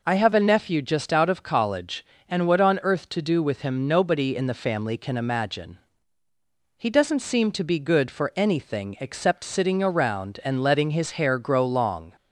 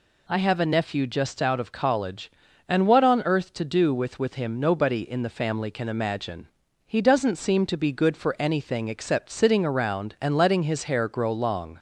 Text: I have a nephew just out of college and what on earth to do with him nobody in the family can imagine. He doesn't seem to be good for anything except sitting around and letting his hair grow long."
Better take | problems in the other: first | says "with" twice; at 4.1 s

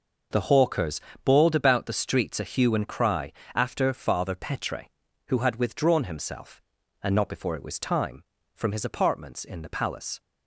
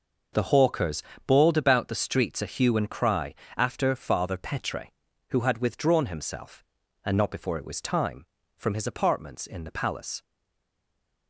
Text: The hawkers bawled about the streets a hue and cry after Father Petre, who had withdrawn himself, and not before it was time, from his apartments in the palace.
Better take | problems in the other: first | pauses between "hawkers" and "bawled"; slight; at 1.0 s; 0.26 s long; slight in the first // pauses between "cry" and "after"; slight; at 3.3 s; 0.22 s long; slight in the first // stays silent after the last word; from 10.2 s on; 1.0 s long

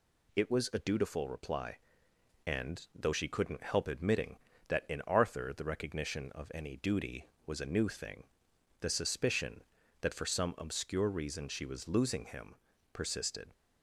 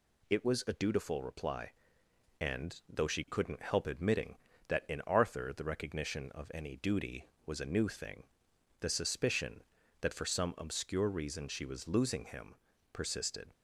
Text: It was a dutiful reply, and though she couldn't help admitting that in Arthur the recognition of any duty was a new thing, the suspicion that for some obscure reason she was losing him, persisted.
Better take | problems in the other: neither | none

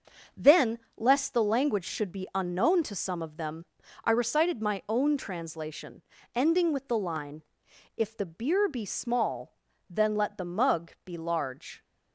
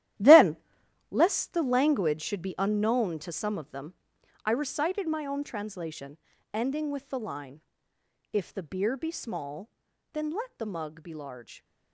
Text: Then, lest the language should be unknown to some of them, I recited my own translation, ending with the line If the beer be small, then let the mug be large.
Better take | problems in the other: first | gets quieter; strong; throughout; 13.5 dB // starts louder than the rest; strong; until 1.7 s; 13 dB; also in the first // pauses between "line" and "If"; noticeable; at 7.6 s; 0.70 s long; noticeable in the first

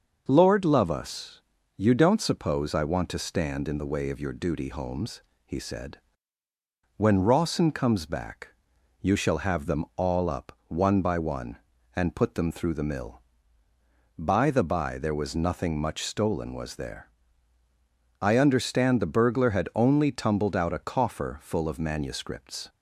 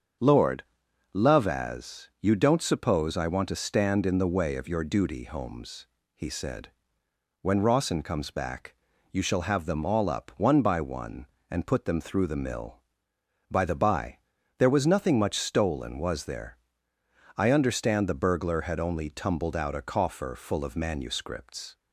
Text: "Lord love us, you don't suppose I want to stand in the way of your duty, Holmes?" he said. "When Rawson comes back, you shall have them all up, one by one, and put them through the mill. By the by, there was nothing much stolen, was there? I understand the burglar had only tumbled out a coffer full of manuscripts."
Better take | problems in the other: first | starts louder than the rest; strong; until 1.7 s; 7 dB; also in the first // pauses between "Lord" and "love"; noticeable; at 0.6 s; 0.54 s long // says "as" for "us"; at 1.4 s

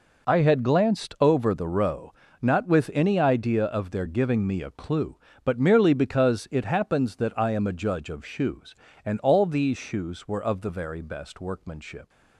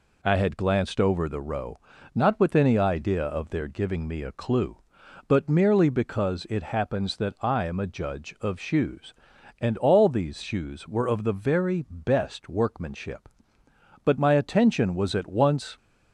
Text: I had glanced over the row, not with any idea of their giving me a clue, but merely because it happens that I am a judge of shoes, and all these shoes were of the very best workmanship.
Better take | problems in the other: first | goes on to say "But my attention was at once"; strong; from 14.0 s on; 1.7 s long

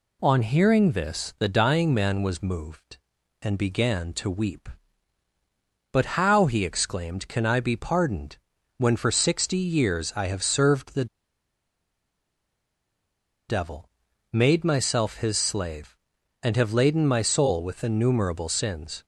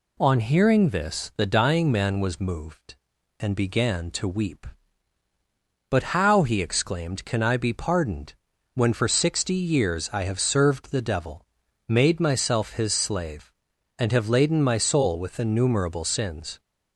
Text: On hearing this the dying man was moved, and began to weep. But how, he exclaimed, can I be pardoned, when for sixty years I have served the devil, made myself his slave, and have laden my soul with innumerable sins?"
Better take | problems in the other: second | pauses between "the" and "devil"; strong; at 11.0 s; 2.4 s long

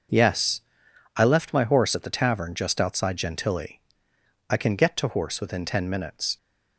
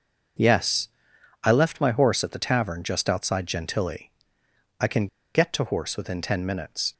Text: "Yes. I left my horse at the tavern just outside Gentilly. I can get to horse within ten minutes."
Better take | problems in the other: first | pauses between "can" and "get"; slight; at 5.0 s; 0.27 s long

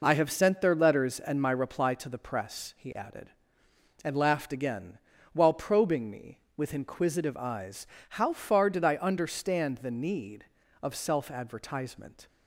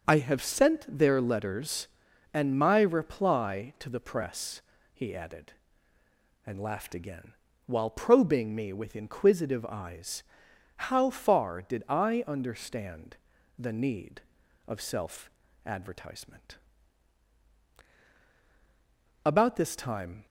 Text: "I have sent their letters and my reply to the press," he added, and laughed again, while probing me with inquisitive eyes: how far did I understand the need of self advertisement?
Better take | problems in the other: first | starts louder than the rest; noticeable; until 1.0 s; 6 dB // pauses between "understand" and "the"; at 13.1 s; 0.42 s long // pauses between "self" and "advertisement"; slight; at 15.3 s; 0.36 s long // goes on to say "About this time"; noticeable; from 19.2 s on; 1.0 s long

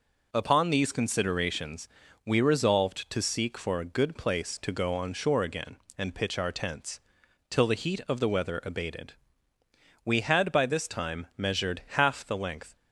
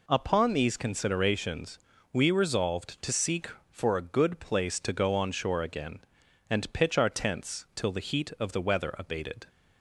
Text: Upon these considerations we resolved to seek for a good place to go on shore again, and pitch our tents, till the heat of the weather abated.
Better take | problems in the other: second | pauses between "considerations" and "we"; slight; at 1.8 s; 0.36 s long; slight in the second // goes on to say "We had by this time measured half the length"; strong; from 10.0 s on; 2.7 s long

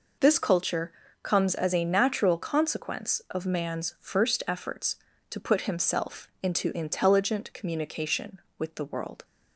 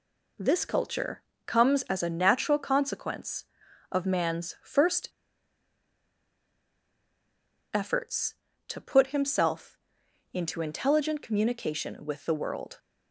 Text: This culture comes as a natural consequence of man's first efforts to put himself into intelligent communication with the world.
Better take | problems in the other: first | pauses between "culture" and "comes"; slight; at 1.2 s; 0.26 s long; slight in the first // pauses between "first" and "efforts"; strong; at 5.0 s; 2.6 s long // pauses between "himself" and "into"; noticeable; at 9.7 s; 0.56 s long

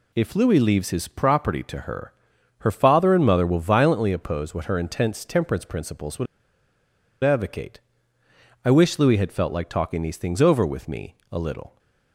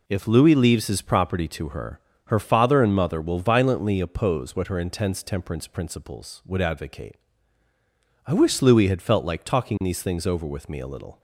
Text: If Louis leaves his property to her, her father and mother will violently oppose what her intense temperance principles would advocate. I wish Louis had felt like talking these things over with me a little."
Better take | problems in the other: second | pauses between "would" and "advocate"; at 6.2 s; 0.98 s long // pauses between "me" and "a"; slight; at 11.1 s; 0.18 s long

